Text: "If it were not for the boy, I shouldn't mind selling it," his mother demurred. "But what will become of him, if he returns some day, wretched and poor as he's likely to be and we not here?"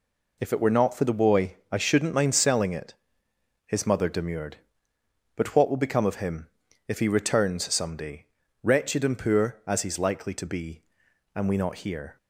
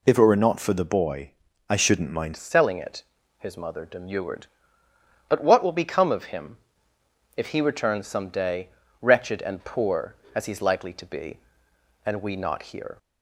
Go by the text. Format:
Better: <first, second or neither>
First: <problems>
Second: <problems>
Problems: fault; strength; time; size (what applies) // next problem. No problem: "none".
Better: first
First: none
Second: changes voice at "selling"; from 2.3 s on; 10.6 s long